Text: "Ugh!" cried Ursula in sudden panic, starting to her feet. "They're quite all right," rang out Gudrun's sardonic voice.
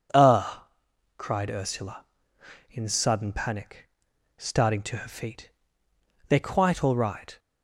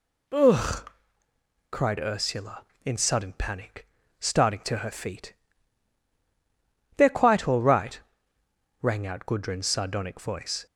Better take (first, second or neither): second